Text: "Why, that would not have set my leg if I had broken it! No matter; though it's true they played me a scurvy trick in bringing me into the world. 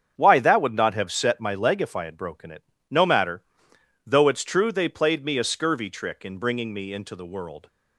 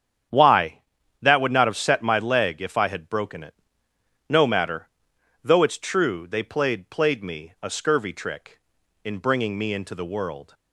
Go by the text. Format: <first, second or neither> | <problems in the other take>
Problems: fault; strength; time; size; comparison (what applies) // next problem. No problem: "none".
first | starts louder than the rest; strong; until 1.7 s; 9 dB; strong in the first // says "played" twice; at 6.8 s